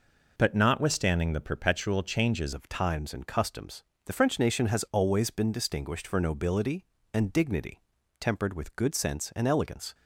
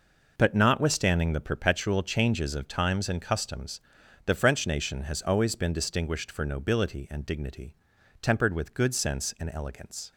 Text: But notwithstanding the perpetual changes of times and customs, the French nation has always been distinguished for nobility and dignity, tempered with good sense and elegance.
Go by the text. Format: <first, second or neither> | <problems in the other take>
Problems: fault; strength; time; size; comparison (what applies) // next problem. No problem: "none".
second | changes voice at "of"; from 2.5 s on; 7.4 s long